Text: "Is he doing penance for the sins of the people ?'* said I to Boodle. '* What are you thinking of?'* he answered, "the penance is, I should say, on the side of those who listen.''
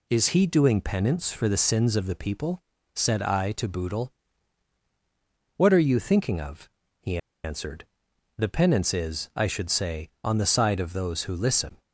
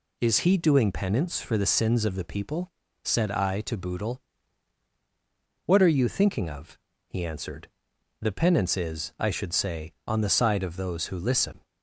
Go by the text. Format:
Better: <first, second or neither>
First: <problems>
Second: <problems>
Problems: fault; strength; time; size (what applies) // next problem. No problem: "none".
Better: second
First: pauses between "he" and "answered"; slight; at 7.1 s; 0.26 s long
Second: none